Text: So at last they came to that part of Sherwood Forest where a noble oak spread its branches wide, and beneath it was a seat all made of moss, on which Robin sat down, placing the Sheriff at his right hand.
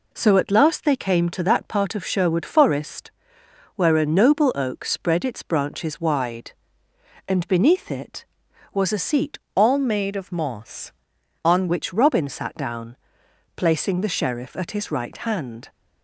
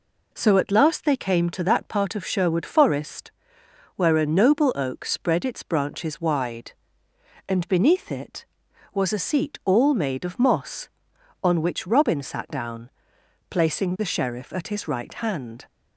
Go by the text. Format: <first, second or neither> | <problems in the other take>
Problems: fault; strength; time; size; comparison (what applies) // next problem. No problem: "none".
second | pauses between "Forest" and "where"; noticeable; at 3.1 s; 0.64 s long; noticeable in the second // changes voice from "all" to "on"; from 9.5 to 11.6 s; 2.1 s long